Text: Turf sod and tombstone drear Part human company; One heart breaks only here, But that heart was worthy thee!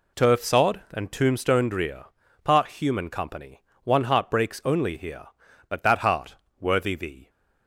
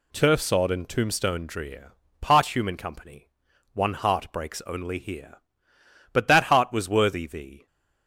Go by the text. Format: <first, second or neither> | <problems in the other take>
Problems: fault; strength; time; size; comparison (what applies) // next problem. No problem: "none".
second | pauses between "drear" and "Part"; at 2.0 s; 0.38 s long; slight in the second // skips "was"; at 6.4 s